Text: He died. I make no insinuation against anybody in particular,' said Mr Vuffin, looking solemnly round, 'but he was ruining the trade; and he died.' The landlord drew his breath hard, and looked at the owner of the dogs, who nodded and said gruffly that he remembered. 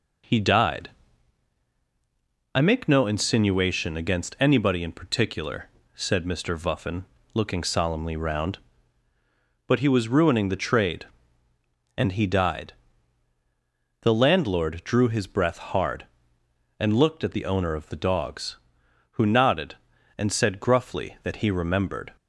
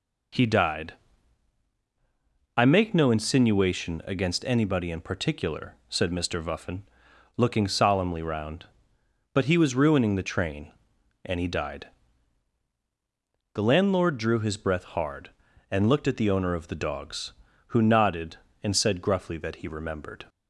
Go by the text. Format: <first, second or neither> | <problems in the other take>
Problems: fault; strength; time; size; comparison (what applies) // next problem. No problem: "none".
first | says "train" for "trade"; at 10.3 s